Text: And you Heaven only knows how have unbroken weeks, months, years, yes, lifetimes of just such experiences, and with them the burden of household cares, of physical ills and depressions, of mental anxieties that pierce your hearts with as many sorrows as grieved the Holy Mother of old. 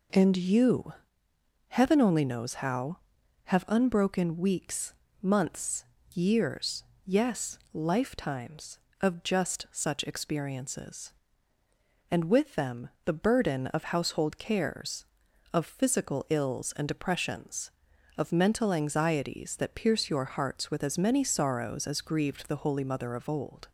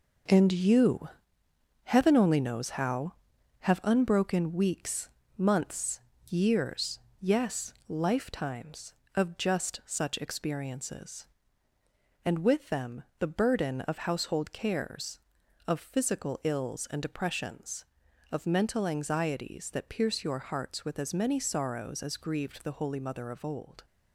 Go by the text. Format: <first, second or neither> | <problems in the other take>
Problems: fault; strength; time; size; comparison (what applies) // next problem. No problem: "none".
first | gets quieter; throughout; 7 dB // pauses between "you" and "Heaven"; noticeable; at 1.0 s; 0.76 s long; noticeable in the first // pauses between "them" and "the"; slight; at 13.0 s; 0.16 s long; slight in the first